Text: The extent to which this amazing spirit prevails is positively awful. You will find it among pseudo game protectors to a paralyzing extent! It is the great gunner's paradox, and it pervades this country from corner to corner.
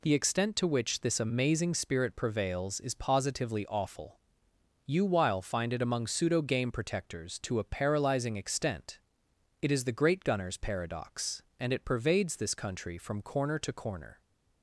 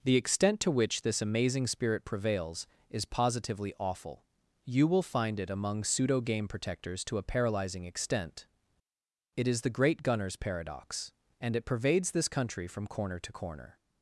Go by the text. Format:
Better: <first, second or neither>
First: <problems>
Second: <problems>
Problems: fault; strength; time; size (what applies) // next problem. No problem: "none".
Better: second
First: says "while" for "will"; at 5.0 s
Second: none